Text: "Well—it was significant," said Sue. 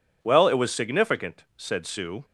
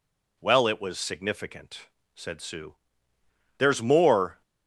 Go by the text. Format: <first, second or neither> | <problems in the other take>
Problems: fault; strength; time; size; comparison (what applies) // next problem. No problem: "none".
first | goes on to say "There's more"; noticeable; from 3.5 s on; 0.84 s long